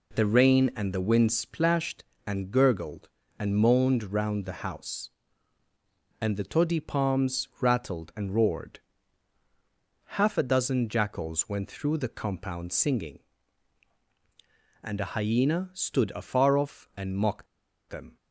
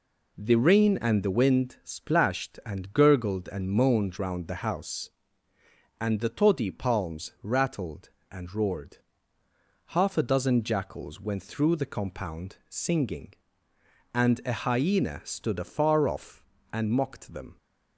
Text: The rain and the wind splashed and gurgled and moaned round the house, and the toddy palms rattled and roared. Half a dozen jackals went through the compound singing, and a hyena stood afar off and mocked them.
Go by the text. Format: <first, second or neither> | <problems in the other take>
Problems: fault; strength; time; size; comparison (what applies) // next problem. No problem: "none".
second | pauses between "mocked" and "them"; at 17.4 s; 0.43 s long